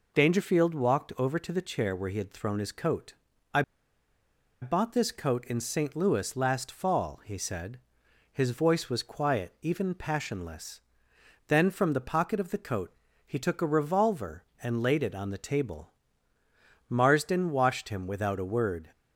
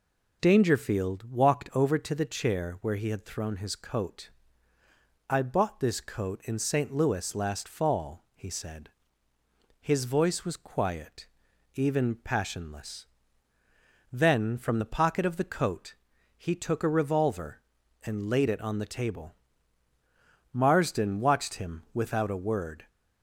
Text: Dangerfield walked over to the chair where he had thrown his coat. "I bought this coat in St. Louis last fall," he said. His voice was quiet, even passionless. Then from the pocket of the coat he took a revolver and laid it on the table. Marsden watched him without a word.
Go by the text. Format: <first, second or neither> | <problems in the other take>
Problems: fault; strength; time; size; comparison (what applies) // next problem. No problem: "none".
second | pauses between "I" and "bought"; at 3.6 s; 1.0 s long // pauses between "coat" and "he"; slight; at 12.9 s; 0.32 s long; also in the second